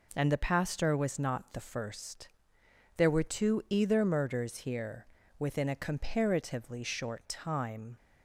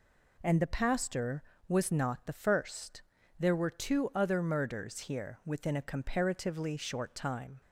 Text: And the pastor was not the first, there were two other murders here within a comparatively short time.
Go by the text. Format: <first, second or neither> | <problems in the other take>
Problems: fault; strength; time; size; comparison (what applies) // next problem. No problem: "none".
second | says "either" for "other"; at 3.6 s // pauses between "here" and "within"; slight; at 5.0 s; 0.32 s long